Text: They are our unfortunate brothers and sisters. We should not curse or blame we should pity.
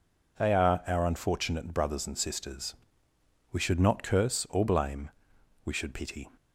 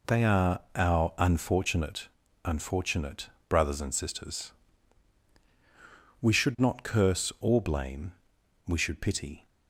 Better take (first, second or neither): first